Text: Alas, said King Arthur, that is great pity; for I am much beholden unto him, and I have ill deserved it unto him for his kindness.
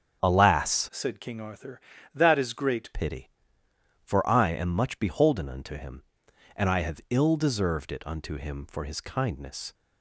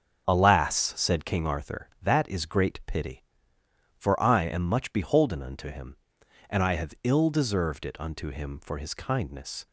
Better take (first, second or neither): second